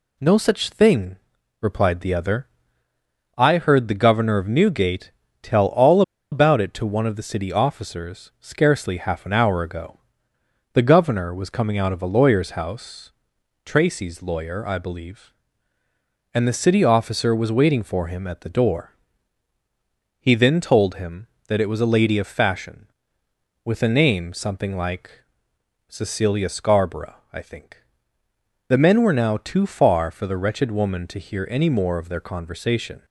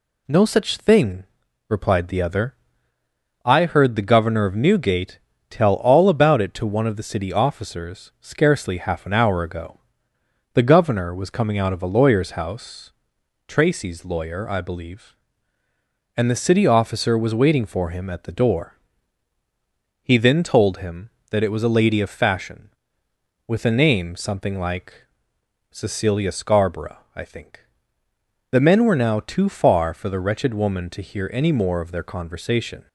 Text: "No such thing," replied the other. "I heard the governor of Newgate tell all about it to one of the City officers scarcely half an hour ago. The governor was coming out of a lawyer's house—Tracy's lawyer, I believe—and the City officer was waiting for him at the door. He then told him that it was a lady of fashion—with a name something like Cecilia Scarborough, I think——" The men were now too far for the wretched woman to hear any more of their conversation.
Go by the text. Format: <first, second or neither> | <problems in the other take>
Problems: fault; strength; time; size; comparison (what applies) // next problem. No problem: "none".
second | pauses between "Newgate" and "tell"; slight; at 5.1 s; 0.32 s long; slight in the second // pauses between "all" and "about"; slight; at 6.0 s; 0.30 s long // pauses between "like" and "Cecilia"; noticeable; at 25.2 s; 0.66 s long; noticeable in the second